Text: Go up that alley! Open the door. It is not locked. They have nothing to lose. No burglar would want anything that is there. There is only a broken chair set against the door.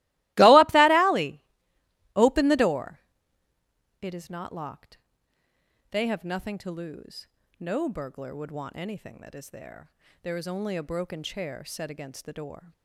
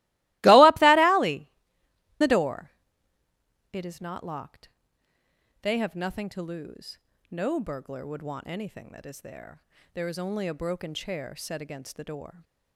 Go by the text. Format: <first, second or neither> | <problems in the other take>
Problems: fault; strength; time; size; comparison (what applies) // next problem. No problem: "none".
first | starts louder than the rest; strong; until 1.4 s; 20.5 dB; strong in the first // skips "Open"; at 1.8 s